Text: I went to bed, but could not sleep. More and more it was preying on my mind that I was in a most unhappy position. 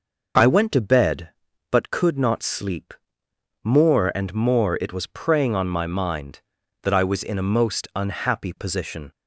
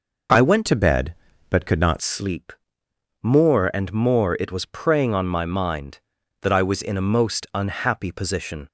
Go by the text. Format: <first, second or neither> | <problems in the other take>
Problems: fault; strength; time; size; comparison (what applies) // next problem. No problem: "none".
first | changes voice from "to" to "not"; from 0.6 to 1.9 s; 1.3 s long